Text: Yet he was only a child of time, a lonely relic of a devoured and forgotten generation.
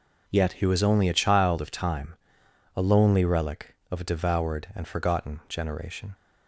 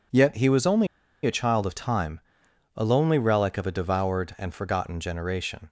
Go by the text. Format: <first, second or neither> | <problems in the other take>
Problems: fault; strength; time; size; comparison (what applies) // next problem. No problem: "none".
first | pauses between "only" and "a"; at 0.8 s; 0.38 s long